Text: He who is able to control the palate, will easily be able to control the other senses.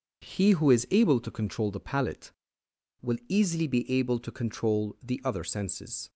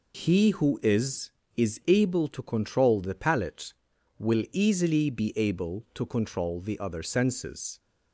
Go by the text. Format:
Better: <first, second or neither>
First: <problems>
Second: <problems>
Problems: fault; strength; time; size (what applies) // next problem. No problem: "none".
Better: first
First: none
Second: says "is" twice; at 1.5 s